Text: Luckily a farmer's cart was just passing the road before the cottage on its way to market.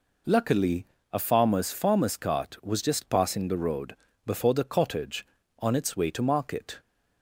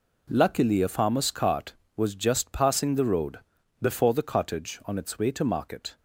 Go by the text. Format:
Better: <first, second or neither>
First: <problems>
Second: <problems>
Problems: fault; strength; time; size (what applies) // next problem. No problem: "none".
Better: second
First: pauses between "Luckily" and "a"; slight; at 0.8 s; 0.26 s long // says "farmer's" twice; at 1.7 s // pauses between "road" and "before"; slight; at 3.9 s; 0.32 s long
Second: pauses between "road" and "before"; at 3.3 s; 0.42 s long